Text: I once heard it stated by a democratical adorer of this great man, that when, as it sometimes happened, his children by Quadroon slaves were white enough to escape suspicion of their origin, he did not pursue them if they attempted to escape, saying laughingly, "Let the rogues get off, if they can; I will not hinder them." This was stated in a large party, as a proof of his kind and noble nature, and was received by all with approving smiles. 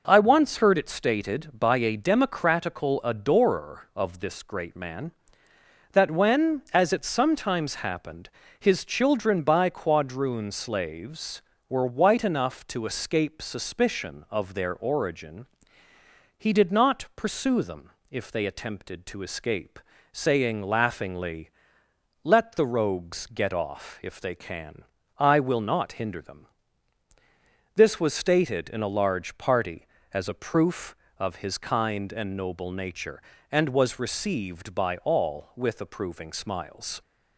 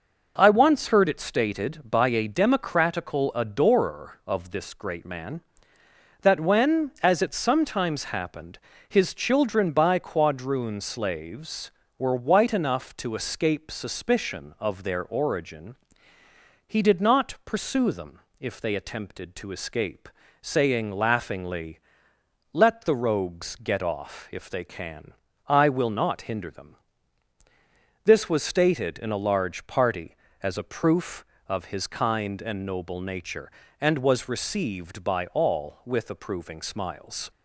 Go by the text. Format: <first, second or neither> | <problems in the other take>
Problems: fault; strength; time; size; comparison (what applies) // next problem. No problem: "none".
neither | pauses between "them" and "if"; slight; the same in both